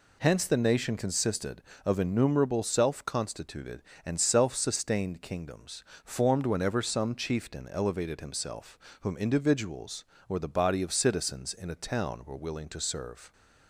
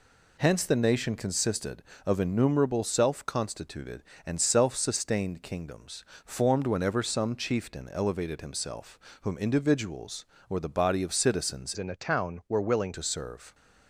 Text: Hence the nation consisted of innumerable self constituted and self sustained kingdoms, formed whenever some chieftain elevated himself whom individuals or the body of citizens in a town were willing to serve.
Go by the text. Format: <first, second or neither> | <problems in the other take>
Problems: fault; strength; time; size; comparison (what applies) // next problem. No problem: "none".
first | pauses between "himself" and "whom"; slight; at 8.9 s; 0.22 s long; slight in the first // changes voice from "in" to "willing"; from 11.7 to 12.9 s; 1.2 s long